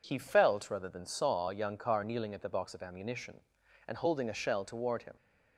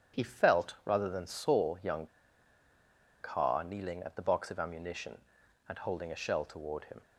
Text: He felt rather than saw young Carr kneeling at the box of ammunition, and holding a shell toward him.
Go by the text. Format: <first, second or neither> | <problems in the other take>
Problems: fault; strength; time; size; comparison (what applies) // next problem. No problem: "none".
first | starts louder than the rest; strong; until 1.2 s; 9 dB // pauses between "young" and "Carr"; at 2.0 s; 1.1 s long